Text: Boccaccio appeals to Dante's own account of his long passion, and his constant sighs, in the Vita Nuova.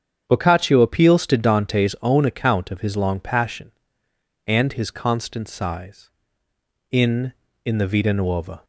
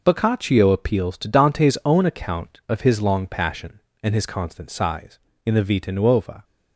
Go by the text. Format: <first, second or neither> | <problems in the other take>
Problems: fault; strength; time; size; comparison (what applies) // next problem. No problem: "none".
second | starts louder than the rest; strong; until 1.2 s; 7.5 dB // says "in" twice; at 7.6 s